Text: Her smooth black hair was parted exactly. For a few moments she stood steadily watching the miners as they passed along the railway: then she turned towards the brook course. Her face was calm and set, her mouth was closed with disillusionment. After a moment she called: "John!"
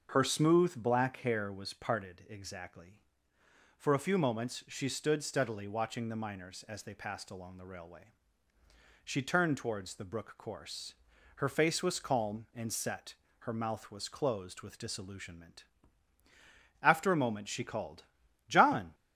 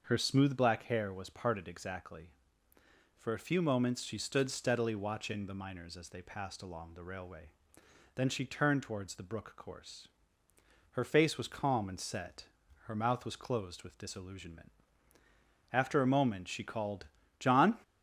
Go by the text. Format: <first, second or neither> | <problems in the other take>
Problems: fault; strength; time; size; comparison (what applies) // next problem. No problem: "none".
second | starts louder than the rest; until 1.1 s; 6.5 dB; also in the second // skips "then"; at 8.5 s